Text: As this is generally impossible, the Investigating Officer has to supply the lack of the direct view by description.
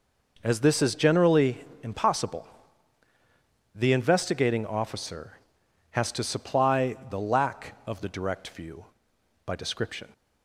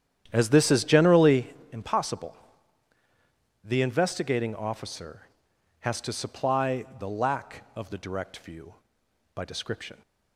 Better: first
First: pauses between "generally" and "impossible"; slight; at 1.5 s; 0.24 s long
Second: starts louder than the rest; strong; until 1.6 s; 10 dB // pauses between "generally" and "impossible"; slight; at 1.4 s; 0.24 s long

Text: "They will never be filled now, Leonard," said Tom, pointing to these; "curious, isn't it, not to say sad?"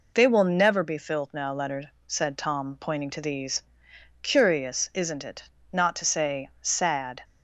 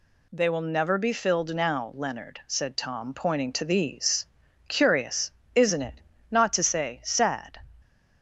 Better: neither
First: none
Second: none

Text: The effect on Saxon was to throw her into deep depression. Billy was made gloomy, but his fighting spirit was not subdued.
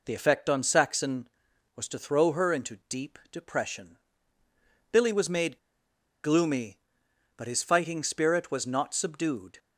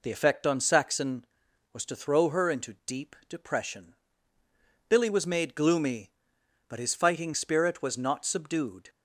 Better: second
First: pauses between "made" and "gloomy"; noticeable; at 5.5 s; 0.65 s long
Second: none

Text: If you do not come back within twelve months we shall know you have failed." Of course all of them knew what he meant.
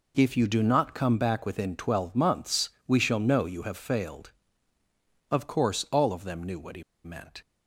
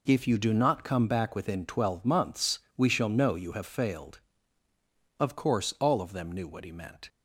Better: second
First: pauses between "months" and "we"; slight; at 2.6 s; 0.18 s long // pauses between "he" and "meant"; slight; at 6.8 s; 0.21 s long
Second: pauses between "months" and "we"; slight; at 2.5 s; 0.18 s long

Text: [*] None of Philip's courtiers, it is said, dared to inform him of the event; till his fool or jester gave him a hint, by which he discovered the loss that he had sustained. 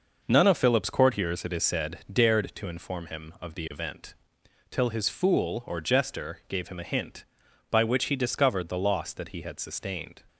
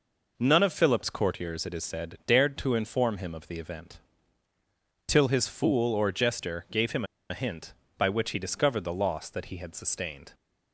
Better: first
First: none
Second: pauses between "him" and "a"; slight; at 7.0 s; 0.23 s long

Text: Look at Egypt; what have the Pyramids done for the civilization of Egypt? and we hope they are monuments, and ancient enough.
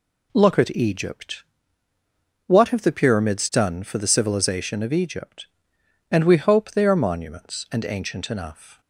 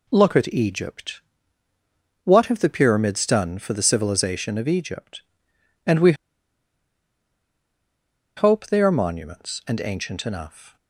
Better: first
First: none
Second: pauses between "we" and "hope"; strong; at 6.1 s; 2.2 s long

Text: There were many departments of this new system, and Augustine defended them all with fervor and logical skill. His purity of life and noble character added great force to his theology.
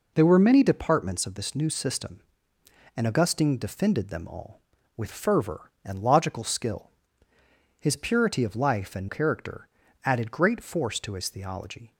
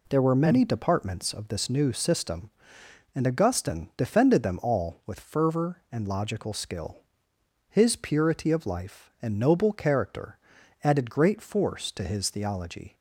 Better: second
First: skips "noble"; at 9.0 s // pauses between "character" and "added"; at 9.6 s; 0.38 s long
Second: pauses between "character" and "added"; noticeable; at 10.3 s; 0.46 s long

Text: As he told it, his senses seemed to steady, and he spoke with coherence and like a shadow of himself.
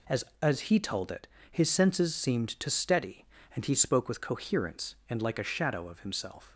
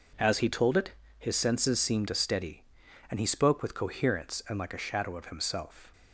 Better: second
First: says "As" twice; at 0.4 s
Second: none

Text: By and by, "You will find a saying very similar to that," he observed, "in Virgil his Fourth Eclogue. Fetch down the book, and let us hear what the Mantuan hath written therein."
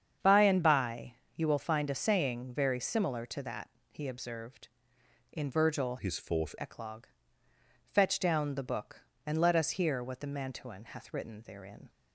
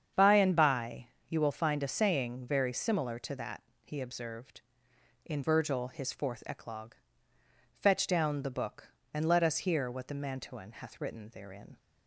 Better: second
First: starts louder than the rest; strong; until 1.4 s; 7.5 dB // changes voice from "his" to "Fourth"; from 5.9 to 6.5 s; 0.6 s long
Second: starts louder than the rest; strong; until 1.3 s; 7.5 dB

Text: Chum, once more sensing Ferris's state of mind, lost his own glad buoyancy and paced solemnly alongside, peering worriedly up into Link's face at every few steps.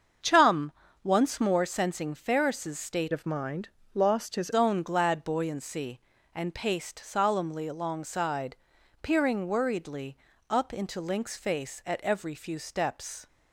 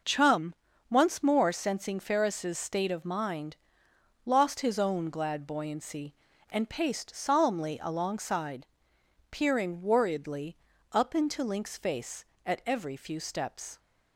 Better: second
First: starts louder than the rest; until 1.5 s; 7 dB // changes voice from "of" to "his"; from 3.1 to 4.5 s; 1.4 s long // pauses between "worriedly" and "up"; slight; at 10.1 s; 0.32 s long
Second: pauses between "worriedly" and "up"; slight; at 10.5 s; 0.34 s long

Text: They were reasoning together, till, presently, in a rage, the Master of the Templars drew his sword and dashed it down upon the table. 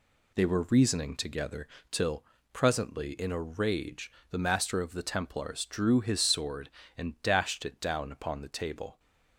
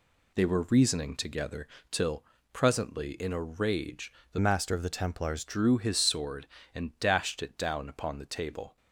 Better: first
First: none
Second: changes voice from "Master" to "Templars"; from 4.3 to 5.4 s; 1.1 s long

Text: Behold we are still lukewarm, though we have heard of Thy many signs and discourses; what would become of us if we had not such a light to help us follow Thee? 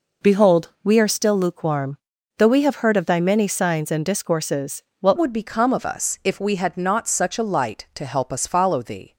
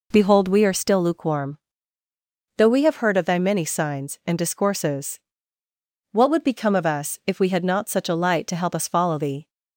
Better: second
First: changes voice at "would"; from 5.1 s on; 4.0 s long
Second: none

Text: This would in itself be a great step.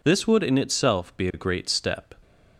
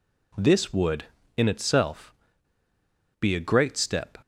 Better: first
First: none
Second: pauses between "itself" and "be"; at 2.1 s; 1.0 s long

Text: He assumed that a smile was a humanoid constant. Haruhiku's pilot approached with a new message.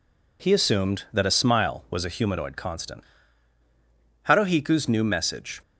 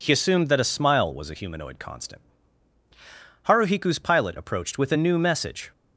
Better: second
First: skips "pilot approached with a"; at 4.8 s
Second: none

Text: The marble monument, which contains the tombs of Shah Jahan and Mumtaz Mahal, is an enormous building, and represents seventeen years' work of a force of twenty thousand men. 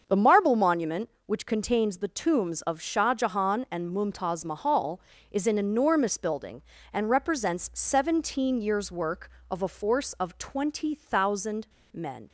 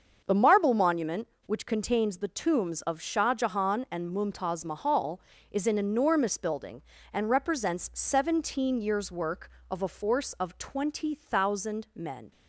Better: second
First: starts louder than the rest; until 1.0 s; 6.5 dB // pauses between "thousand" and "men"; slight; at 11.6 s; 0.24 s long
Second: starts louder than the rest; until 1.2 s; 6.5 dB

